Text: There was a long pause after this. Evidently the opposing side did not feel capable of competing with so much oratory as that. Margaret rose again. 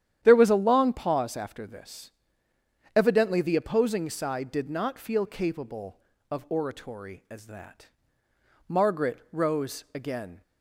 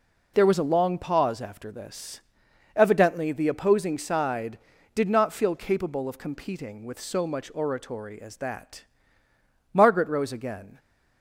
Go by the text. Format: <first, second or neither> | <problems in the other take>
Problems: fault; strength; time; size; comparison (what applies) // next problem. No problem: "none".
second | starts louder than the rest; strong; until 1.2 s; 10.5 dB // skips "competing with so much"; at 6.4 s